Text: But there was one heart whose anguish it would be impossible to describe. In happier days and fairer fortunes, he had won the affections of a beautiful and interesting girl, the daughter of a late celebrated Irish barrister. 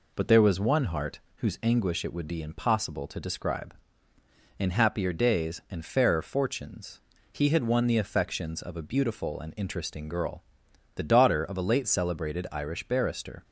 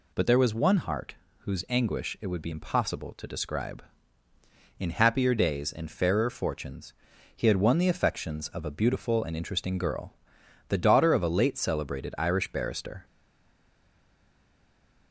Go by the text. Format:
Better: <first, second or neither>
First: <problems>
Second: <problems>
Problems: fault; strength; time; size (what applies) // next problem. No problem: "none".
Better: first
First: pauses between "heart" and "whose"; slight; at 1.1 s; 0.18 s long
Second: pauses between "heart" and "whose"; slight; at 1.1 s; 0.24 s long // stays silent after the last word; noticeable; from 13.0 s on; 2.1 s long